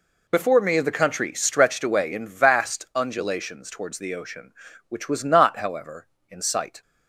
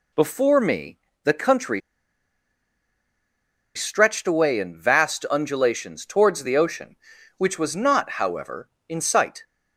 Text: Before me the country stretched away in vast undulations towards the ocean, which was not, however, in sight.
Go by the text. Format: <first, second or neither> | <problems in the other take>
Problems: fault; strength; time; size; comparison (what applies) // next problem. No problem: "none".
first | pauses between "me" and "the"; slight; at 0.9 s; 0.26 s long // pauses between "country" and "stretched"; strong; at 1.8 s; 1.9 s long